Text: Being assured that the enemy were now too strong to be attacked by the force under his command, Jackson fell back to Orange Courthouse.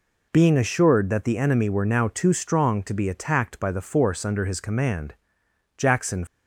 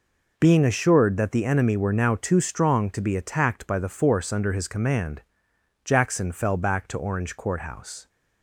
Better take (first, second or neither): second